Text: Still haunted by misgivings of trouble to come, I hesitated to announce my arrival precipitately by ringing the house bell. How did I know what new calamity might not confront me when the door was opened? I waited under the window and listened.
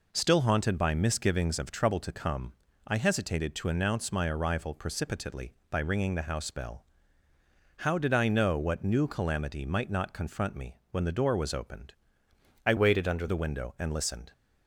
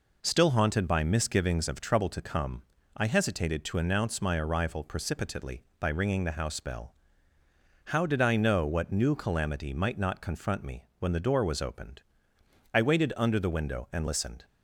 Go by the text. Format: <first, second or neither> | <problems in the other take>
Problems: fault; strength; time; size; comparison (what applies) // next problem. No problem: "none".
second | pauses between "me" and "when"; slight; at 10.7 s; 0.16 s long; slight in the second // changes voice from "waited" to "under"; from 12.7 to 13.2 s; 0.5 s long